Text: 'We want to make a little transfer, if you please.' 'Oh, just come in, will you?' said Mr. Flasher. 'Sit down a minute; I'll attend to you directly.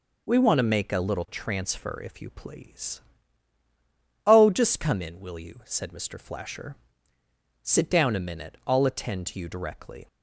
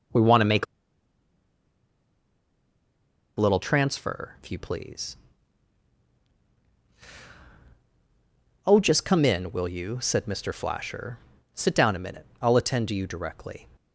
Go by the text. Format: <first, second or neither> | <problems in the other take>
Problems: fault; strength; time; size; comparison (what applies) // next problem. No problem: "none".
first | starts louder than the rest; until 3.8 s; 6.5 dB // pauses between "make" and "a"; strong; at 0.6 s; 2.7 s long